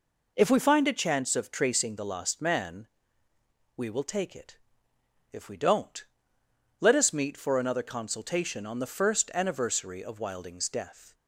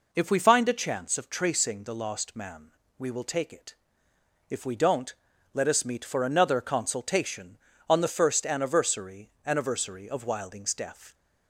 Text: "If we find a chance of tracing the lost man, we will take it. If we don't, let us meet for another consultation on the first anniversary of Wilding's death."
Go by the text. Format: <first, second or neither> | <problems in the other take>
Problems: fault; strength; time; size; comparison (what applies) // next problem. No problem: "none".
first | says "anniversary" twice; at 9.4 s